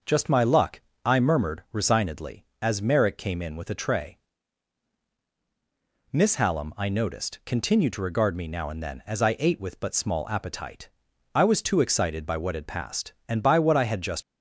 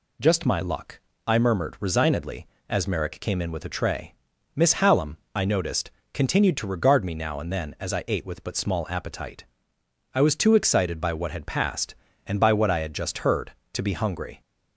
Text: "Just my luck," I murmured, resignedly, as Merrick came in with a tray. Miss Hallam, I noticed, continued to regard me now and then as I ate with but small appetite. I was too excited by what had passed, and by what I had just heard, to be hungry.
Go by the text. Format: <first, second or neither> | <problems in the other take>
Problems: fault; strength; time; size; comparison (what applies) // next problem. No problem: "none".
second | stops before "heard to be hungry"; at 14.2 s